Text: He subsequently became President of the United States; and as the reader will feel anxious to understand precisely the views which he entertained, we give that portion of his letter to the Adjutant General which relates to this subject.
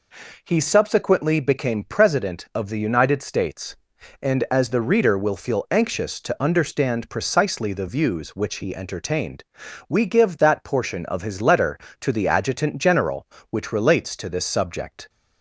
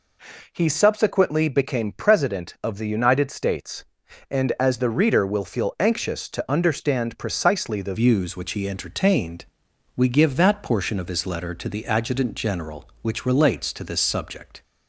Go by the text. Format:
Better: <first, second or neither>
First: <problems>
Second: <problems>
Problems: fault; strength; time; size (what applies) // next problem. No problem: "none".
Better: first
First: none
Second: changes voice at "views"; from 7.9 s on; 6.7 s long